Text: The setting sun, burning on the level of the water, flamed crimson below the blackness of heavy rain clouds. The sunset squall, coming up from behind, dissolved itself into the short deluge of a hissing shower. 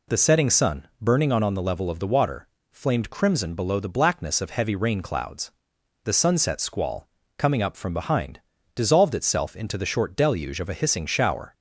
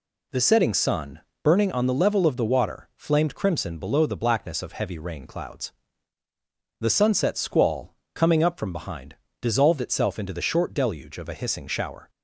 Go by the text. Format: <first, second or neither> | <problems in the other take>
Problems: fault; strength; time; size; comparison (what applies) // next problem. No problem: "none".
second | says "on" twice; at 1.4 s